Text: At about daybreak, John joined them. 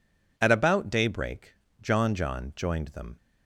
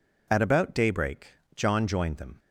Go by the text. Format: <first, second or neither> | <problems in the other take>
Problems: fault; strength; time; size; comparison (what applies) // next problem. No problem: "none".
second | says "John" twice; at 2.1 s